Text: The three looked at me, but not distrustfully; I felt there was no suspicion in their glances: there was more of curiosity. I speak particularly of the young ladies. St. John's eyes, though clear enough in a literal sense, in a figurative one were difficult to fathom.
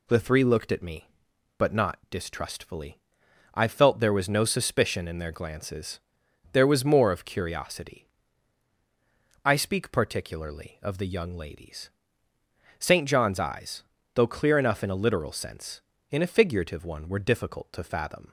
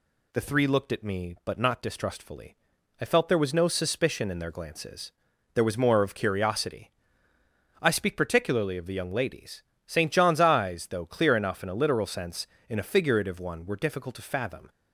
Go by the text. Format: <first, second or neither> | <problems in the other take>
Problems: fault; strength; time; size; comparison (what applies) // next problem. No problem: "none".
neither | none